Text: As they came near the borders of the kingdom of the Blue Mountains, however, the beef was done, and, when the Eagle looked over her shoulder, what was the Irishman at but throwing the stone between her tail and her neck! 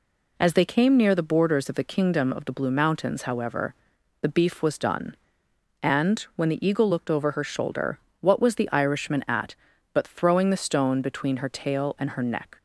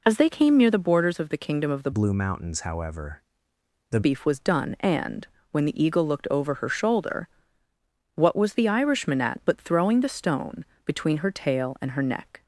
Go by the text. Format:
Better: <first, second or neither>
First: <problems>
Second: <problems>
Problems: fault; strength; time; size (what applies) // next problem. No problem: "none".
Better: first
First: none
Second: changes voice from "Blue" to "the"; from 1.9 to 4.0 s; 2.1 s long // pauses between "stone" and "between"; slight; at 10.6 s; 0.18 s long